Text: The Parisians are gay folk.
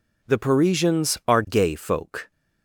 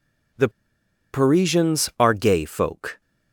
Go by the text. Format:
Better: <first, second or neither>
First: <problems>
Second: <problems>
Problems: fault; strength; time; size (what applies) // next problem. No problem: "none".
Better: first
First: none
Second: pauses between "The" and "Parisians"; noticeable; at 0.4 s; 0.64 s long